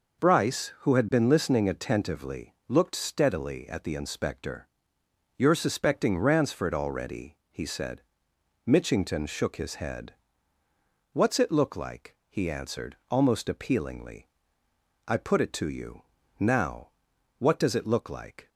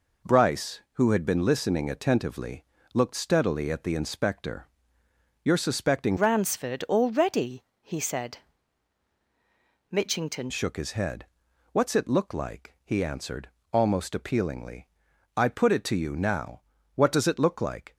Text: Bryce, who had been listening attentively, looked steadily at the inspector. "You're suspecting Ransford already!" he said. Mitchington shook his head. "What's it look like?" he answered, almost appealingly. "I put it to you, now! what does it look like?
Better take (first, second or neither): first